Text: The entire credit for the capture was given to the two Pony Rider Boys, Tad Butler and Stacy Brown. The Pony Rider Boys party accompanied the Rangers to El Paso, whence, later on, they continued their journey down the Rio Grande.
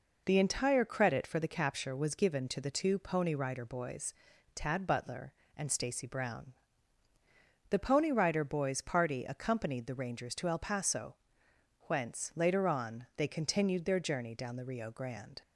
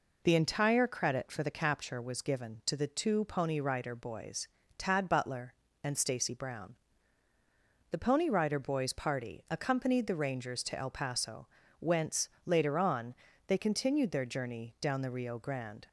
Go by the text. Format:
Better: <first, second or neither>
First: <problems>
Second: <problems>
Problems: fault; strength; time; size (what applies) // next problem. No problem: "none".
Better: neither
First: none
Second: none